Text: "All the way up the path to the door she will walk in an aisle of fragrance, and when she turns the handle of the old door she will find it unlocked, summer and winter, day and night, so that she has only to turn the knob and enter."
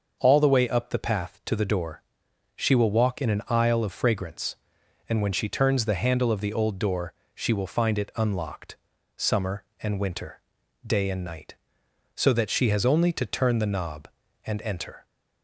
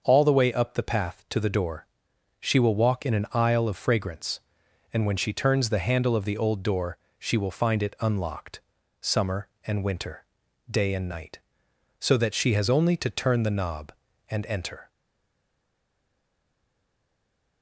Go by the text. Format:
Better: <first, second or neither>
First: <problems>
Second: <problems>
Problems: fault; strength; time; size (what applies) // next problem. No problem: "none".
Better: first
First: starts louder than the rest; until 1.2 s; 6.5 dB // pauses between "door" and "she"; noticeable; at 2.0 s; 0.54 s long // pauses between "door" and "she"; slight; at 7.1 s; 0.24 s long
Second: starts louder than the rest; until 1.0 s; 6.5 dB // pauses between "door" and "she"; noticeable; at 1.8 s; 0.54 s long // pauses between "door" and "she"; slight; at 6.9 s; 0.24 s long // stays silent after the last word; strong; from 14.8 s on; 2.8 s long